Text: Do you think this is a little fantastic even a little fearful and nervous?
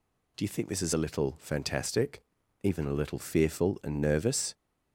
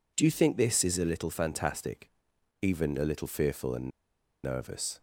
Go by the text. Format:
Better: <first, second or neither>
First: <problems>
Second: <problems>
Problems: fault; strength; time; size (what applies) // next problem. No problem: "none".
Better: first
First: pauses between "fantastic" and "even"; at 2.2 s; 0.41 s long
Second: pauses between "fantastic" and "even"; noticeable; at 2.1 s; 0.50 s long // pauses between "and" and "nervous"; noticeable; at 3.8 s; 0.54 s long